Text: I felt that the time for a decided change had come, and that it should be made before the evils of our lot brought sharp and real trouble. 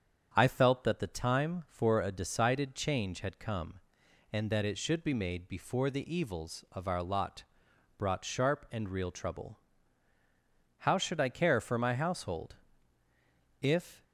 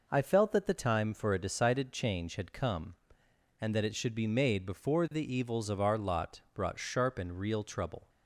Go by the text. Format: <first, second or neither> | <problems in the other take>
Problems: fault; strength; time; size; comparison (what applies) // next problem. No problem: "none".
second | starts louder than the rest; strong; until 1.3 s; 8 dB // pauses between "lot" and "brought"; noticeable; at 7.4 s; 0.54 s long // goes on to say "How should I care for my household If"; strong; from 10.7 s on; 3.2 s long